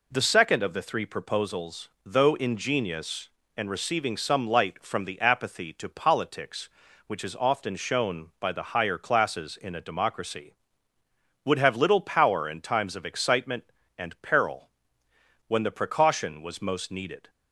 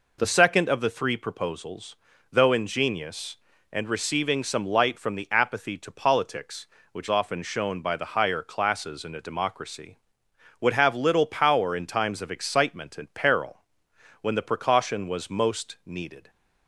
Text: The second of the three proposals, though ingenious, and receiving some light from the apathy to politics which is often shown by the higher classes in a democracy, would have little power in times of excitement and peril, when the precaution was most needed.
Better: first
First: none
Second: skips "is"; at 7.0 s

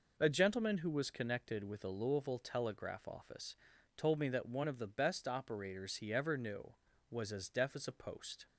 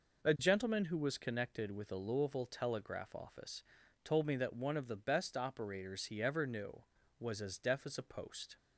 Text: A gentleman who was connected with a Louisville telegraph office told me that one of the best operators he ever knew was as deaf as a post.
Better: neither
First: pauses between "office" and "told"; at 3.5 s; 0.40 s long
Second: pauses between "office" and "told"; at 3.6 s; 0.40 s long

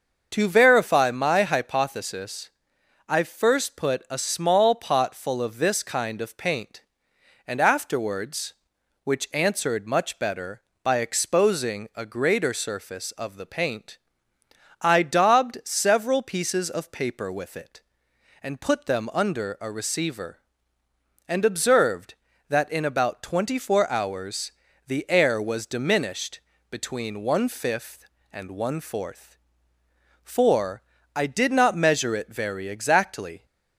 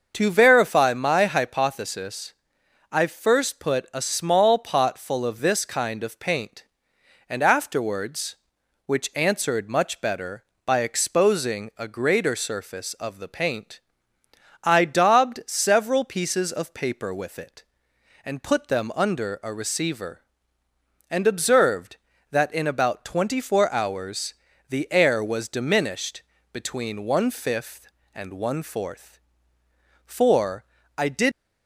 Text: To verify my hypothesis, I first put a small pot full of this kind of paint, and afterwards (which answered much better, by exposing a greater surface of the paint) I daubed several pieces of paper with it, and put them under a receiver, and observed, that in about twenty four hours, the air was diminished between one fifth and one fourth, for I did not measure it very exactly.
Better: first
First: starts louder than the rest; until 1.3 s; 6.5 dB // pauses between "diminished" and "between"; slight; at 26.3 s; 0.30 s long // pauses between "for" and "I"; slight; at 30.8 s; 0.32 s long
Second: starts louder than the rest; until 1.1 s; 6.5 dB // pauses between "diminished" and "between"; slight; at 26.2 s; 0.30 s long // pauses between "for" and "I"; slight; at 30.6 s; 0.32 s long // stops before "not measure it very exactly"; at 31.3 s

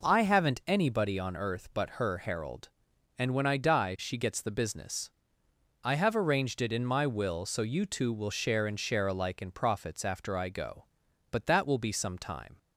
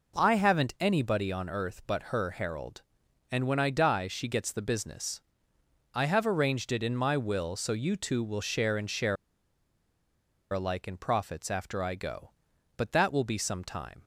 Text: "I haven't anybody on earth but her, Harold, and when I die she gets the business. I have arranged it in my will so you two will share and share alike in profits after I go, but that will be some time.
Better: first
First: none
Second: pauses between "share" and "alike"; strong; at 9.1 s; 1.3 s long

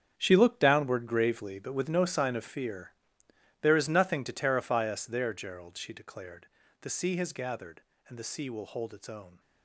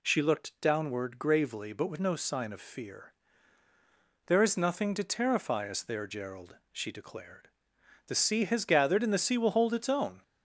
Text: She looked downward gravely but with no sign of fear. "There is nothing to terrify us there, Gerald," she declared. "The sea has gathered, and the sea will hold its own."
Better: second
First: gets quieter; strong; throughout; 13 dB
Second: none

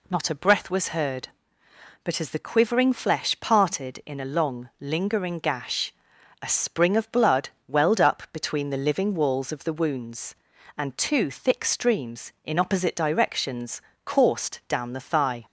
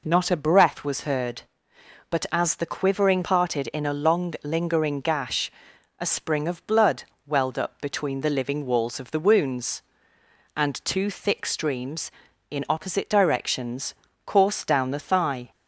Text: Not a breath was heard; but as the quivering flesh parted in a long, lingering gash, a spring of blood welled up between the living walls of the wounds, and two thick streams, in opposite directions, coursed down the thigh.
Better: first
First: pauses between "blood" and "welled"; slight; at 7.4 s; 0.20 s long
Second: skips "flesh"; at 3.2 s // pauses between "blood" and "welled"; slight; at 7.0 s; 0.24 s long

